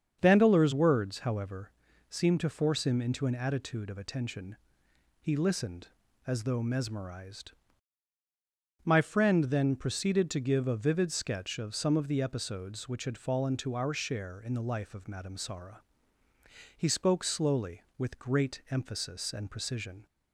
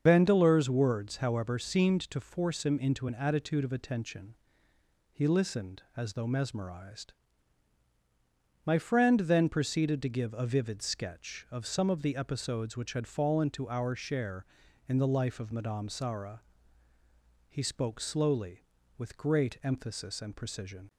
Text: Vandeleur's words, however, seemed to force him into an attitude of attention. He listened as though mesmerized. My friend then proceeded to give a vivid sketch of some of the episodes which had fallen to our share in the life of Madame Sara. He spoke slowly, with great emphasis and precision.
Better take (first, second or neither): first